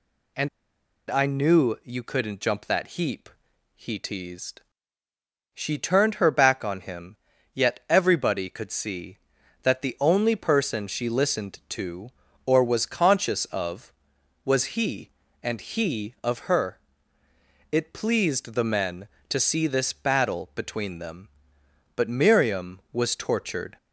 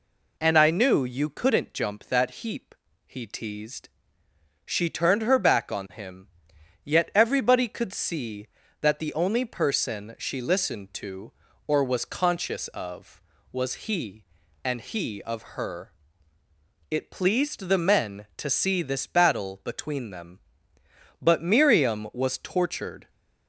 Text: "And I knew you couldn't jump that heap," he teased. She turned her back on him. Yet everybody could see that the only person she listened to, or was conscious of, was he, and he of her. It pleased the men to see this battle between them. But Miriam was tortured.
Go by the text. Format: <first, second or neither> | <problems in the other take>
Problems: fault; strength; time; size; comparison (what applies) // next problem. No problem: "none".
second | pauses between "And" and "I"; noticeable; at 0.4 s; 0.62 s long